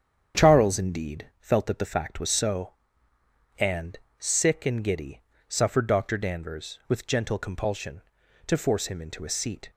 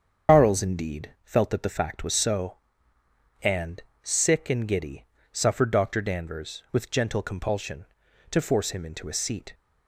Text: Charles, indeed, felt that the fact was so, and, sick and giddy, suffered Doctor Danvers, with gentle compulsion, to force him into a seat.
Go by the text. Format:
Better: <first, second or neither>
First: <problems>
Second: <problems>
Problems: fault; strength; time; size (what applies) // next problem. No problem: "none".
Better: first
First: starts louder than the rest; strong; until 1.4 s; 8 dB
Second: loses the start of "Charles"; at 0.2 s; 105 ms // starts louder than the rest; strong; until 1.3 s; 7.5 dB